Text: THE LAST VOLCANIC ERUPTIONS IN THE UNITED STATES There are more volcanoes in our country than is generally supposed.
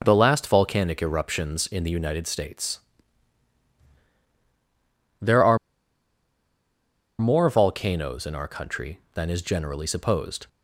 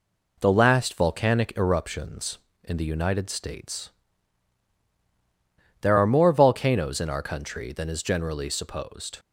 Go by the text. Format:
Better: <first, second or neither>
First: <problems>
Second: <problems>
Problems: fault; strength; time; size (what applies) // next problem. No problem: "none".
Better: second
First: pauses between "STATES" and "There"; strong; at 2.8 s; 2.4 s long // pauses between "are" and "more"; strong; at 5.5 s; 1.6 s long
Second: pauses between "STATES" and "There"; strong; at 3.8 s; 1.9 s long